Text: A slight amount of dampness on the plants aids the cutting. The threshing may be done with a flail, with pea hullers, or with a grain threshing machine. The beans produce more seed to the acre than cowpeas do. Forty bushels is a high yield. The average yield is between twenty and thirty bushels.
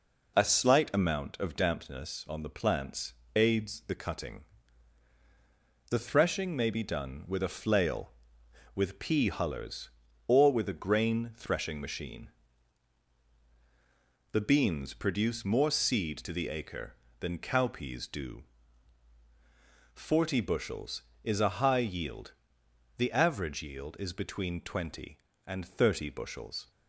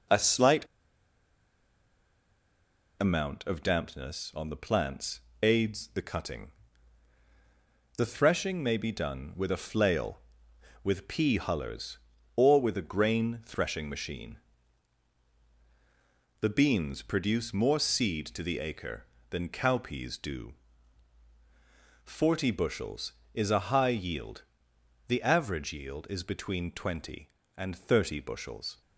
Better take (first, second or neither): first